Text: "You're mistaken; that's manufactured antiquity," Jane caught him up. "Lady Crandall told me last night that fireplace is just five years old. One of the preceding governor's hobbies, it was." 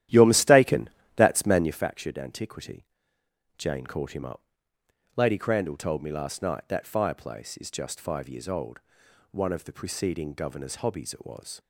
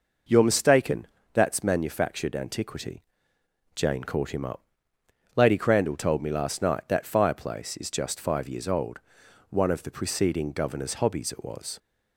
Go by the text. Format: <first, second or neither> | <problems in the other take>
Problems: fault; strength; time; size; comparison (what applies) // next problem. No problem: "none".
second | starts louder than the rest; strong; until 1.9 s; 12.5 dB